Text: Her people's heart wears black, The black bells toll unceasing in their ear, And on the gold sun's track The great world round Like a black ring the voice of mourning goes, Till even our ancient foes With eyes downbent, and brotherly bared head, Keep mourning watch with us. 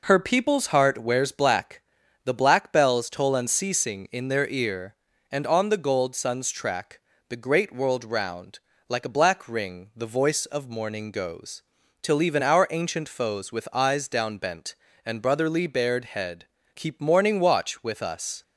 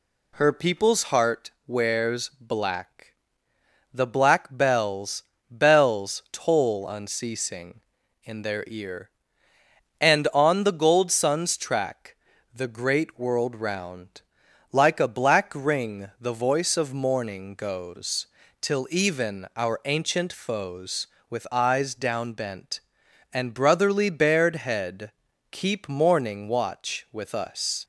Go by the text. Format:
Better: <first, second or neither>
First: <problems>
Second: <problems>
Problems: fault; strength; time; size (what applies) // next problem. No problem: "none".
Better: first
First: pauses between "track" and "The"; slight; at 7.0 s; 0.30 s long // pauses between "round" and "Like"; slight; at 8.5 s; 0.32 s long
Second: pauses between "heart" and "wears"; slight; at 1.5 s; 0.16 s long // says "bells" twice; at 5.4 s // pauses between "track" and "The"; slight; at 12.1 s; 0.36 s long // pauses between "round" and "Like"; noticeable; at 14.2 s; 0.50 s long